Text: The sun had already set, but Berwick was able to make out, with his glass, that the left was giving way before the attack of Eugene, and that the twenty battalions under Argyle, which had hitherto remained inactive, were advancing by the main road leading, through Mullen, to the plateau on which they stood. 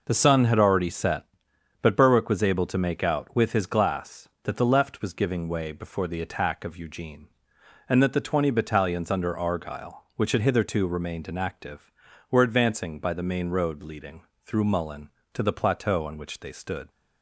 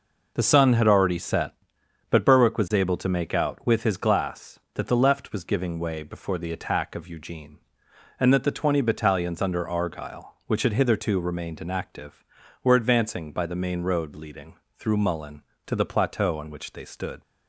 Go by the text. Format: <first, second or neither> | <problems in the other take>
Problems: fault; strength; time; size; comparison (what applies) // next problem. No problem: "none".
neither | none